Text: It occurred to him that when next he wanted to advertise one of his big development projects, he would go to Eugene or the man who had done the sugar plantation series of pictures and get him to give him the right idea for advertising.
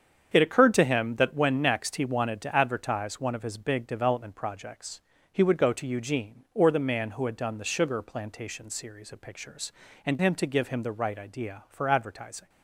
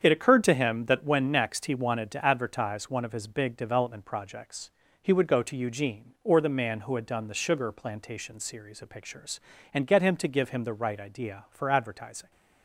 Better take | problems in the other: second | starts louder than the rest; strong; until 1.3 s; 7.5 dB; strong in the second // skips "get"; at 10.1 s

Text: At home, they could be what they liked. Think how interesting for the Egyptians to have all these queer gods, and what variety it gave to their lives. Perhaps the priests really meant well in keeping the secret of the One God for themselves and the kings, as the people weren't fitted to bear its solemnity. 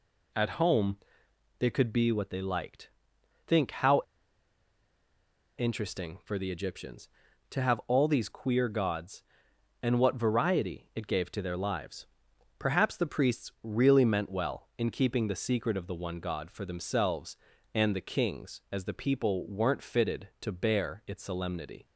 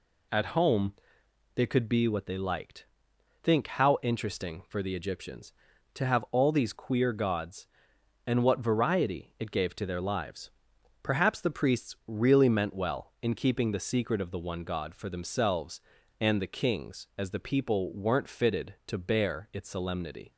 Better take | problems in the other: second | pauses between "how" and "interesting"; strong; at 4.0 s; 1.5 s long

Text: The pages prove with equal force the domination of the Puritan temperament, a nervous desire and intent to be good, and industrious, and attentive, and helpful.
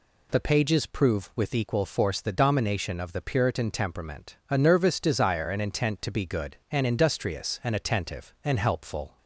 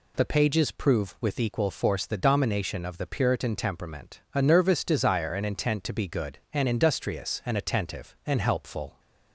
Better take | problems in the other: neither | none

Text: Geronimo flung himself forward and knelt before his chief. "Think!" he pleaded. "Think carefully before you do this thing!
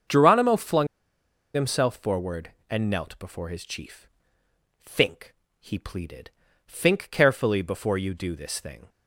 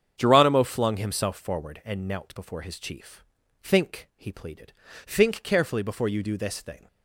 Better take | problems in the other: second | starts louder than the rest; until 1.7 s; 7 dB; strong in the second // pauses between "flung" and "himself"; noticeable; at 0.8 s; 0.67 s long

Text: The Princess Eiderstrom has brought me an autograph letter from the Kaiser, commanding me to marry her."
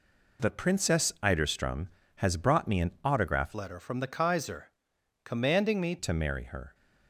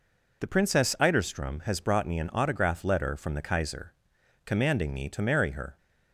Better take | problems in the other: second | changes voice from "letter" to "me"; from 3.5 to 5.9 s; 2.4 s long

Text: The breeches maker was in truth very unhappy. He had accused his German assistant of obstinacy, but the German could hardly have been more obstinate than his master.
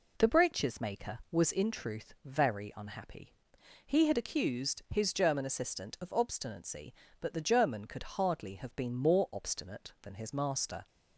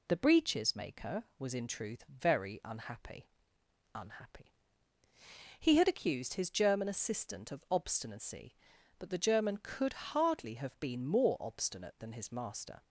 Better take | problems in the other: first | says "unhappy" twice; at 3.9 s

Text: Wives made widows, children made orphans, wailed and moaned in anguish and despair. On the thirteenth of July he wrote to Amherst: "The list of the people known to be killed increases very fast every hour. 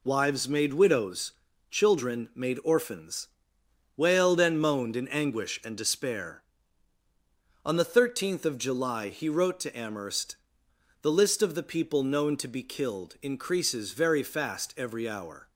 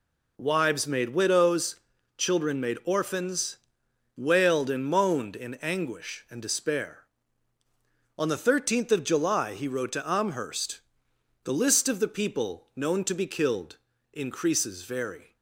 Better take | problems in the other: first | pauses between "killed" and "increases"; slight; at 13.7 s; 0.34 s long // stops before "fast every hour"; at 15.3 s

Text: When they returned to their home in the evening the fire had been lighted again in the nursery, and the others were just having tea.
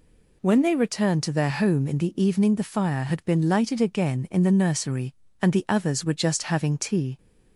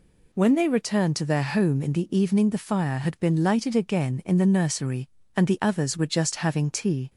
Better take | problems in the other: neither | none

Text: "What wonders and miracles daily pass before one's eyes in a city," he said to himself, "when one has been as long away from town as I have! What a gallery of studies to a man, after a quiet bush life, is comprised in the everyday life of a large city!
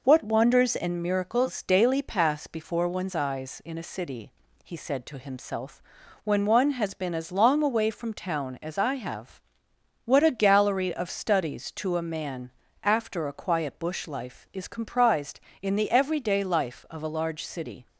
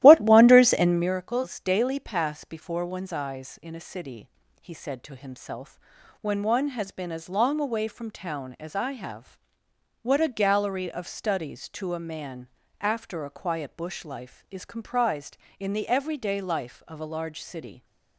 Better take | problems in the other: first | starts louder than the rest; strong; until 1.1 s; 14 dB

